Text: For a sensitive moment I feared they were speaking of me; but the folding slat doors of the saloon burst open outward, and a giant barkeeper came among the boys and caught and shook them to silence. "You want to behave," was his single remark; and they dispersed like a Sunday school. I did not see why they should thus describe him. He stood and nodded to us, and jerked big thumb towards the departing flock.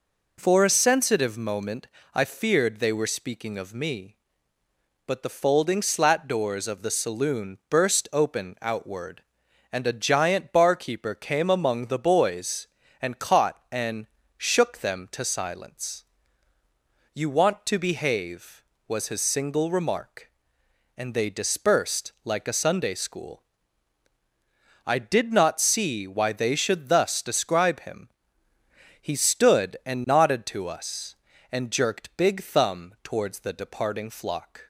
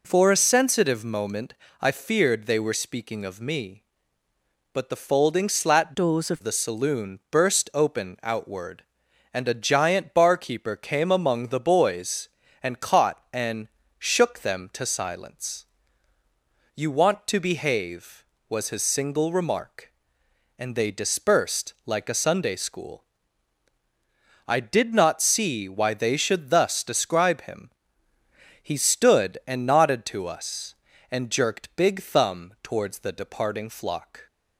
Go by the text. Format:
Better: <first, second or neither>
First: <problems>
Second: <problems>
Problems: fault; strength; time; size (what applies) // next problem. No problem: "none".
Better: first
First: pauses between "moment" and "I"; slight; at 1.8 s; 0.28 s long // pauses between "and" and "shook"; slight; at 14.0 s; 0.30 s long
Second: pauses between "moment" and "I"; slight; at 1.5 s; 0.28 s long // changes voice from "doors" to "of"; from 5.9 to 6.4 s; 0.5 s long // pauses between "and" and "shook"; slight; at 13.6 s; 0.30 s long